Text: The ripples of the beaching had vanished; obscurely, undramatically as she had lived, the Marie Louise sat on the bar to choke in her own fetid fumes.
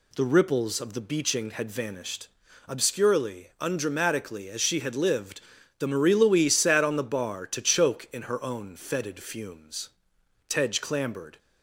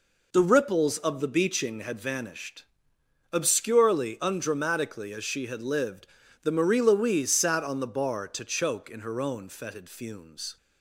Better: second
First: goes on to say "Tedge clambered"; noticeable; from 10.4 s on; 0.88 s long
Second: none

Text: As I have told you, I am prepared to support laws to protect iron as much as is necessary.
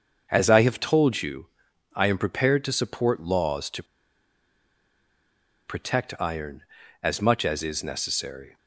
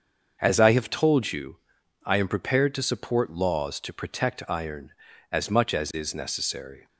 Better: second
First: starts louder than the rest; until 1.3 s; 7 dB // pauses between "to" and "protect"; strong; at 3.8 s; 1.8 s long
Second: starts louder than the rest; until 1.4 s; 7 dB

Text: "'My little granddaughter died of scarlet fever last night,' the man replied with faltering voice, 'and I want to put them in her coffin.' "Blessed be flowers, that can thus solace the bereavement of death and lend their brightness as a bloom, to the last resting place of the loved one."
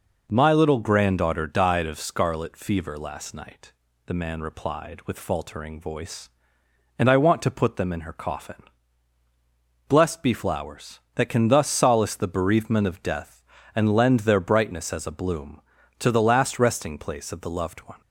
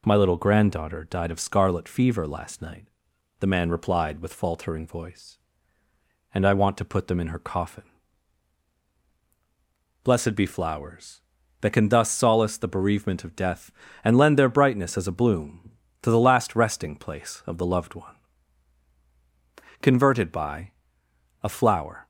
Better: first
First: none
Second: goes on to say "CONVERTED BY A FLOWER"; strong; from 19.8 s on; 2.2 s long

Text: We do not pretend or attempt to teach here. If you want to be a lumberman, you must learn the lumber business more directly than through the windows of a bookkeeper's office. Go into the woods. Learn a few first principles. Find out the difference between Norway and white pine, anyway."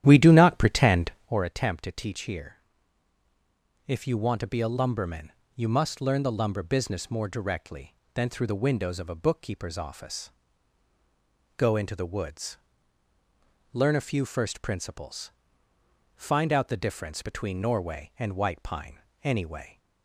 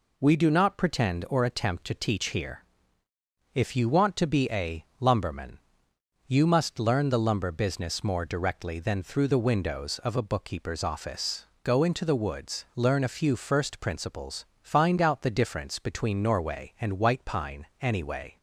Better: second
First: starts louder than the rest; strong; until 1.5 s; 11.5 dB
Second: none

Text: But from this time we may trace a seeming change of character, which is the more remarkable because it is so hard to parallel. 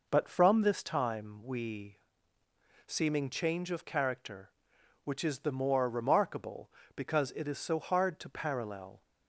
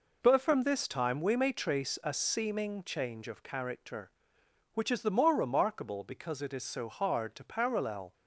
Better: second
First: skips "may trace a"; at 2.4 s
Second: none

